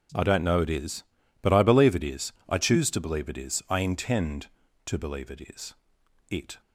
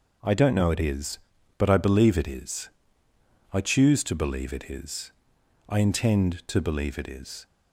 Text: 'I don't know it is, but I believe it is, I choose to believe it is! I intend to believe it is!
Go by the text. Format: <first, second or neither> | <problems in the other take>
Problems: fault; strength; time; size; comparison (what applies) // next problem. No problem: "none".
second | goes on to say "It"; slight; from 6.2 s on; 0.32 s long